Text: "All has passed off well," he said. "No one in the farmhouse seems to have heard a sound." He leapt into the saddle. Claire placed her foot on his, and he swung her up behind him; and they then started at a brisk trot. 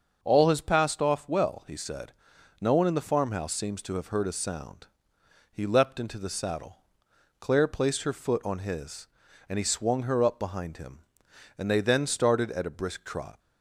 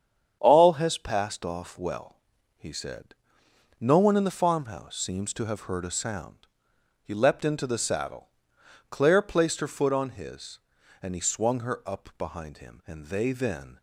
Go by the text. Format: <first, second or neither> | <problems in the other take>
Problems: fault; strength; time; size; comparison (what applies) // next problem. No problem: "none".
first | starts louder than the rest; strong; until 1.4 s; 8.5 dB; also in the first // stops before "started at a brisk trot"; at 13.7 s